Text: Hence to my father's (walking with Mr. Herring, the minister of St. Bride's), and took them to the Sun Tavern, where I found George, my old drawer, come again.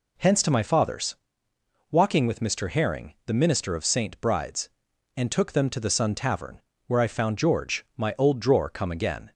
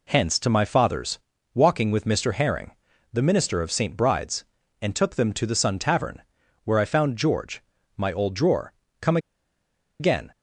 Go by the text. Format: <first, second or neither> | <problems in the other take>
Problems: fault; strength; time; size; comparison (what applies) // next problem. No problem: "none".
first | pauses between "come" and "again"; noticeable; at 9.1 s; 0.82 s long